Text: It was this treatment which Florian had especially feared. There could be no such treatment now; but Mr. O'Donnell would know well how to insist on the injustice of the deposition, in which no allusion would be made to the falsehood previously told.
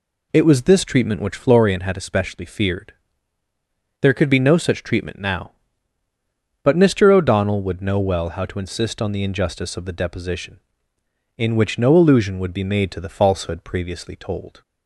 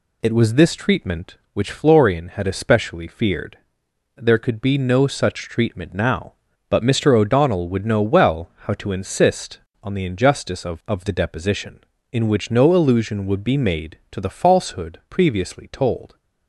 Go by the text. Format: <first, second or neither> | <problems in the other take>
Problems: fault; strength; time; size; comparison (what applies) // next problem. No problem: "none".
first | says "of" twice; at 10.8 s